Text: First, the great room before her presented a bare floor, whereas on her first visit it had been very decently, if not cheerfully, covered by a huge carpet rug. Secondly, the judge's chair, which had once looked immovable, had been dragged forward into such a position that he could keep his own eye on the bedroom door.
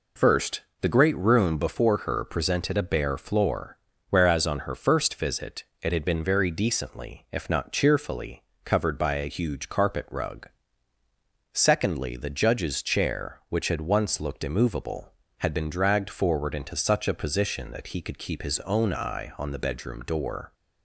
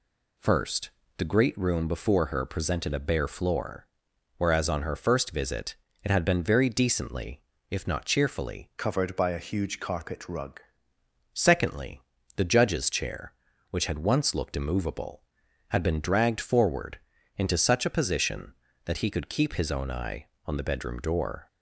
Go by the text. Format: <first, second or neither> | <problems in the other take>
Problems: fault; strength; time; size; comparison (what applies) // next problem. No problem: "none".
first | pauses between "visit" and "it"; slight; at 5.7 s; 0.30 s long; slight in the first // changes voice from "covered" to "rug"; from 8.7 to 10.5 s; 1.8 s long // pauses between "forward" and "into"; at 16.9 s; 0.38 s long